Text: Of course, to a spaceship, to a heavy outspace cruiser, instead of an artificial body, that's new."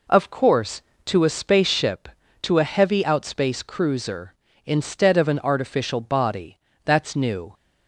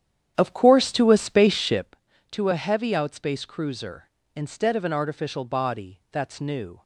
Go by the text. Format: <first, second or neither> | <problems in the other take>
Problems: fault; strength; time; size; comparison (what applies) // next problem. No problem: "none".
first | starts louder than the rest; strong; until 1.9 s; 10 dB